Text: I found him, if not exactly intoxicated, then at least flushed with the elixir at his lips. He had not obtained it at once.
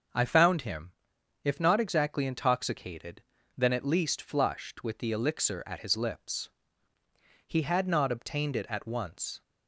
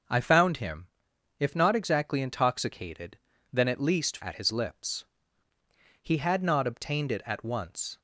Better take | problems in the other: first | starts louder than the rest; noticeable; until 1.5 s; 6 dB; noticeable in the first // skips "flushed with the elixir"; at 4.2 s

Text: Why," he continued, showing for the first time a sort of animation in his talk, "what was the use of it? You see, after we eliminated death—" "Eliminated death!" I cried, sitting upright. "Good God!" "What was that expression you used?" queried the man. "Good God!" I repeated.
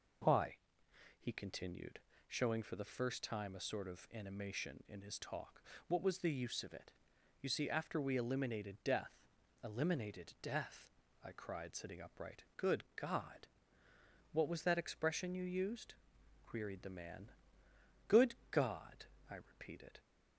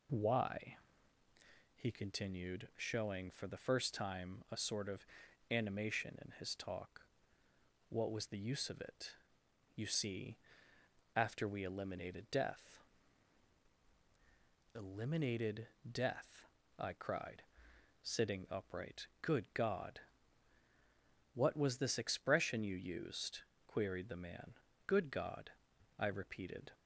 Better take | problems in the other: first | pauses between "of" and "animation"; at 5.0 s; 0.42 s long // pauses between "Eliminated" and "death"; slight; at 15.6 s; 0.20 s long // says "this" for "that"; at 21.7 s

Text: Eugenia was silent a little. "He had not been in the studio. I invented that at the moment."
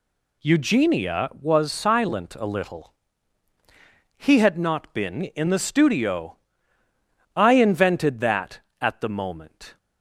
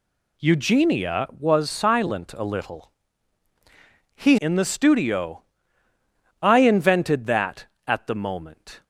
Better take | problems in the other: first | skips "had not been"; at 4.3 s

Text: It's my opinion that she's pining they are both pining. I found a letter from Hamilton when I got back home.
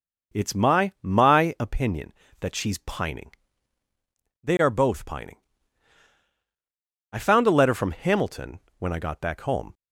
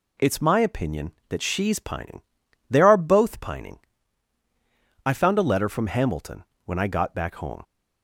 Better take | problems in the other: second | says "my" twice; at 1.0 s // pauses between "pining" and "they"; at 3.3 s; 1.1 s long; noticeable in the second // pauses between "Hamilton" and "when"; slight; at 8.5 s; 0.18 s long; slight in the second

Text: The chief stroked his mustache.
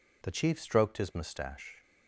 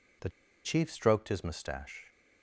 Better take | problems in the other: first | pauses between "The" and "chief"; slight; at 0.2 s; 0.34 s long

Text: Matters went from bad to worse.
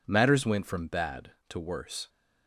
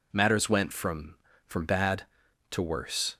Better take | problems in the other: first | says "from" twice; at 1.4 s

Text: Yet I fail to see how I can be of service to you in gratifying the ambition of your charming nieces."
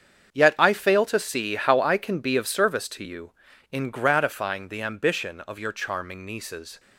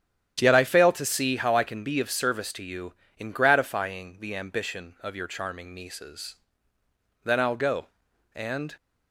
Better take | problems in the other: first | starts louder than the rest; strong; until 1.4 s; 10 dB; strong in the first // goes on to say "Then I'll go and"; from 7.1 s on; 1.5 s long

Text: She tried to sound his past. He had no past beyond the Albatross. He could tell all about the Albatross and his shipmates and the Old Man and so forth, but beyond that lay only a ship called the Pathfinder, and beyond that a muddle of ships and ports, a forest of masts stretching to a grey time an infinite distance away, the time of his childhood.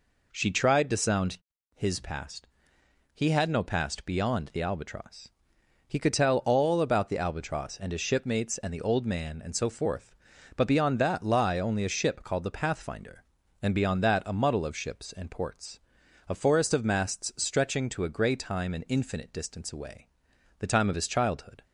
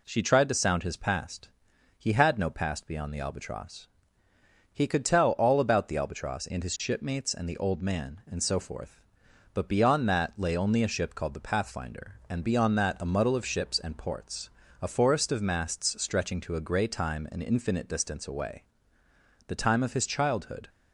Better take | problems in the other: second | pauses between "sound" and "his"; at 1.3 s; 0.38 s long // says "lie" for "lay"; at 11.2 s

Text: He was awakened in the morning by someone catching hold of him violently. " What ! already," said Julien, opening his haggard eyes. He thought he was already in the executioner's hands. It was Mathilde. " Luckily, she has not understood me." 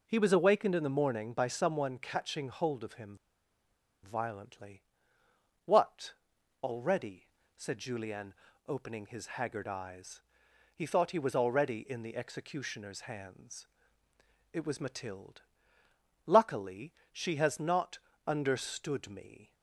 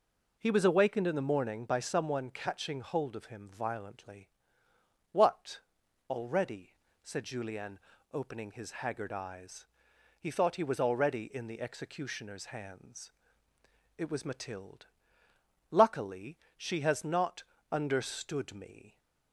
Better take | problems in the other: second | pauses between "him" and "violently"; noticeable; at 3.1 s; 0.86 s long // pauses between "not" and "understood"; slight; at 17.9 s; 0.30 s long; slight in the second

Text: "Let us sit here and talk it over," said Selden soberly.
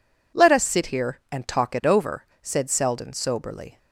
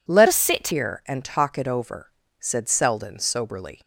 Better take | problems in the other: first | changes voice from "us" to "sit"; from 0.2 to 0.6 s; 0.4 s long

